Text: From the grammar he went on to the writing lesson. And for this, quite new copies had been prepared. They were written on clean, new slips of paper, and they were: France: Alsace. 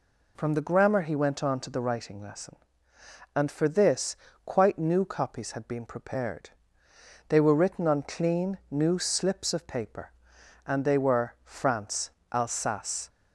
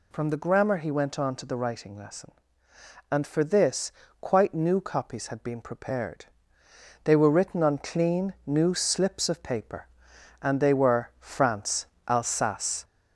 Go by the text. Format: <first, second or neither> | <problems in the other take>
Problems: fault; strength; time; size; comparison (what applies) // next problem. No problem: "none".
first | gets louder; noticeable; throughout; 4 dB